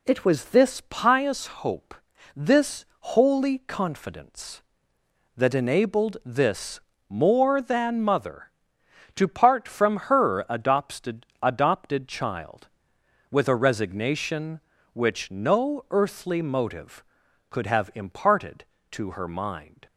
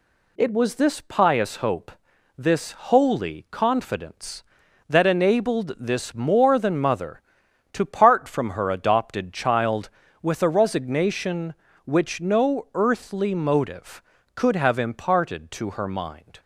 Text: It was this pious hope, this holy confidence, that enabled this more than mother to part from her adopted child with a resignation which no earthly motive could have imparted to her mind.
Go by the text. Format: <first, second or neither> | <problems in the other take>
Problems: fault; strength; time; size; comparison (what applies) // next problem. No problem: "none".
second | pauses between "this" and "holy"; slight; at 2.8 s; 0.16 s long // pauses between "this" and "more"; slight; at 6.8 s; 0.28 s long // says "adopted" twice; at 11.4 s